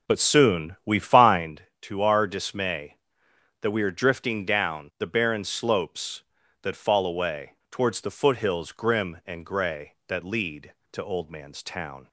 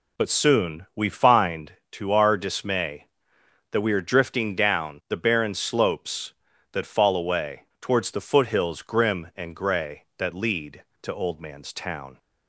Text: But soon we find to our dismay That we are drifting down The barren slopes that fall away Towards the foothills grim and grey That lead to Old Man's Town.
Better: second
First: starts louder than the rest; noticeable; until 1.5 s; 5.5 dB // pauses between "away" and "Towards"; slight; at 7.5 s; 0.20 s long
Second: pauses between "away" and "Towards"; slight; at 7.6 s; 0.20 s long

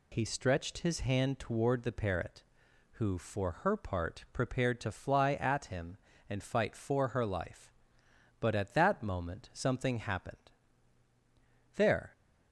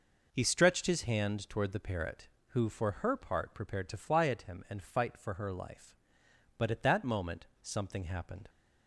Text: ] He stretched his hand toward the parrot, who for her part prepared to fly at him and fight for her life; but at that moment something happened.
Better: second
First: goes on to say "There"; slight; from 11.7 s on; 0.36 s long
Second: none

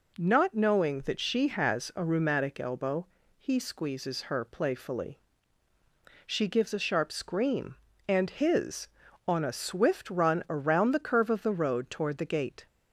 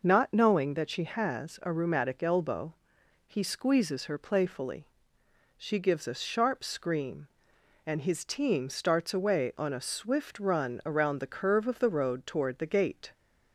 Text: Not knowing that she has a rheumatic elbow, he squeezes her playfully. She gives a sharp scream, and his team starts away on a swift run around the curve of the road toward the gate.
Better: second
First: skips "team starts away"; at 9.0 s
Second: none

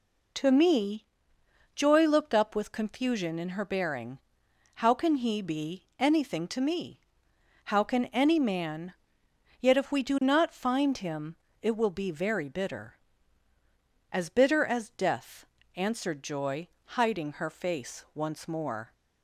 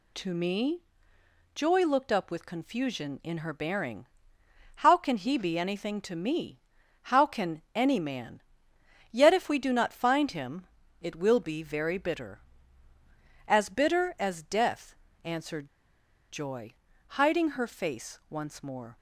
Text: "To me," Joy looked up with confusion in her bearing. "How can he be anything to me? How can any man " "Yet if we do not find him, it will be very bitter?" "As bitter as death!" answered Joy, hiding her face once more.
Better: first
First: none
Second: pauses between "answered" and "Joy"; noticeable; at 15.6 s; 0.61 s long

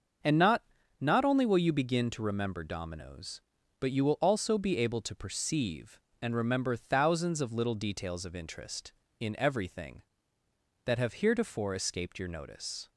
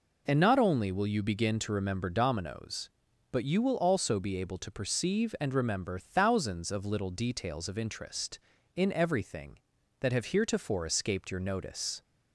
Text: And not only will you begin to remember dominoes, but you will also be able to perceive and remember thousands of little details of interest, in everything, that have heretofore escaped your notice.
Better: second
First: starts louder than the rest; until 1.5 s; 6.5 dB // says "not" twice; at 0.9 s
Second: none

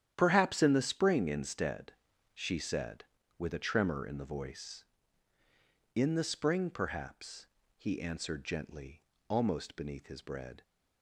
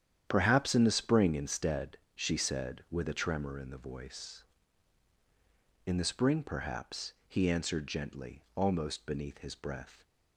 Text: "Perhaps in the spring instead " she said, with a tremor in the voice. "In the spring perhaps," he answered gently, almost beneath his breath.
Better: second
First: starts louder than the rest; strong; until 1.1 s; 9.5 dB // says "bread" for "breath"; at 10.2 s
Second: starts louder than the rest; strong; until 1.2 s; 9.5 dB

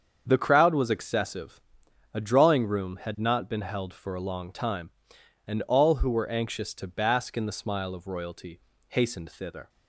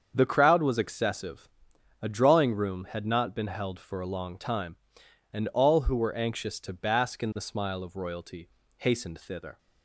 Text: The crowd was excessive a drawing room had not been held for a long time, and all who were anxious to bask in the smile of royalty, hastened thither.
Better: neither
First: starts louder than the rest; strong; until 1.2 s; 7 dB // pauses between "excessive" and "a"; noticeable; at 1.6 s; 0.52 s long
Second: starts louder than the rest; strong; until 1.1 s; 7 dB // pauses between "excessive" and "a"; noticeable; at 1.4 s; 0.52 s long

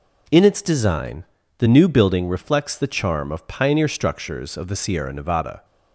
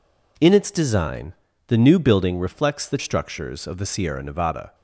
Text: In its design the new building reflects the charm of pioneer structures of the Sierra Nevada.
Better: first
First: pauses between "design" and "the"; slight; at 1.2 s; 0.34 s long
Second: pauses between "design" and "the"; slight; at 1.3 s; 0.34 s long // skips "charm of pioneer"; at 2.9 s

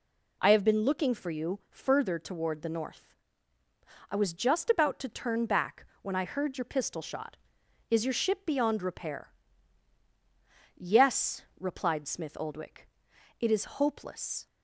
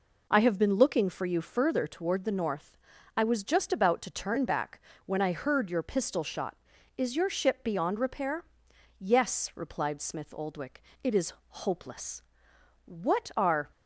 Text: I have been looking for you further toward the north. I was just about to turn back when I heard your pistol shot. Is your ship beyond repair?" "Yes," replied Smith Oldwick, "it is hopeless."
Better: first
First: pauses between "back" and "when"; slight; at 5.8 s; 0.16 s long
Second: pauses between "back" and "when"; slight; at 4.7 s; 0.26 s long // pauses between "is" and "hopeless"; slight; at 11.3 s; 0.18 s long // goes on to say "What are"; noticeable; from 12.8 s on; 0.84 s long

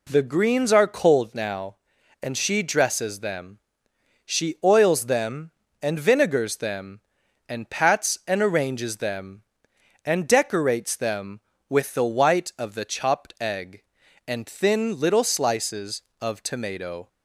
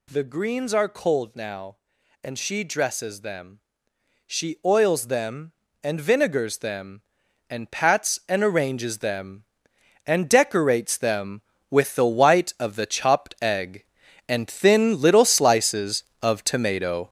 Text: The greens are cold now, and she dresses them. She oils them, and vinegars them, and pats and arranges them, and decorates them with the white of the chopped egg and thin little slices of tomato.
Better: first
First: none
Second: gets louder; strong; throughout; 7 dB

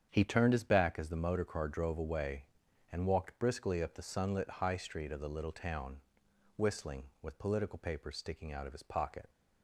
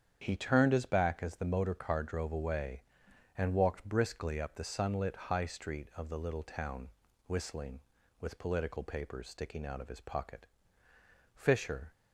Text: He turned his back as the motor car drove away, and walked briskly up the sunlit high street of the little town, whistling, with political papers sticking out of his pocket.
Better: first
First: starts louder than the rest; strong; until 1.1 s; 8 dB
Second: starts louder than the rest; strong; until 1.2 s; 8.5 dB // goes on to say "Fisher"; from 11.3 s on; 0.58 s long

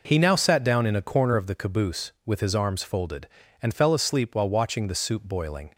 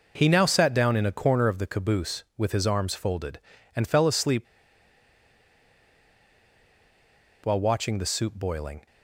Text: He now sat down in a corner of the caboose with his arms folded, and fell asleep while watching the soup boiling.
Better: first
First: none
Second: pauses between "asleep" and "while"; strong; at 4.4 s; 3.0 s long

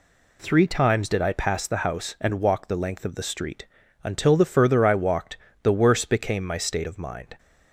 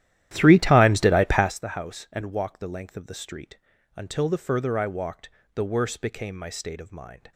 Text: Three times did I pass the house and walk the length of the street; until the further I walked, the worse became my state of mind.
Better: first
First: none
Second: starts louder than the rest; strong; until 1.5 s; 12.5 dB

